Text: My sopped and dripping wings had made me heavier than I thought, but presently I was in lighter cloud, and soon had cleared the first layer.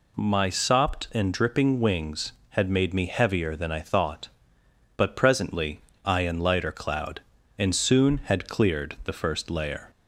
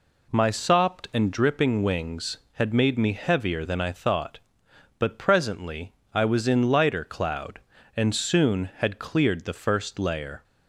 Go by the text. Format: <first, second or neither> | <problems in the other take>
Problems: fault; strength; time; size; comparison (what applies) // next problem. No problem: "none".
second | pauses between "presently" and "I"; slight; at 5.8 s; 0.24 s long; slight in the second // skips "was"; at 6.2 s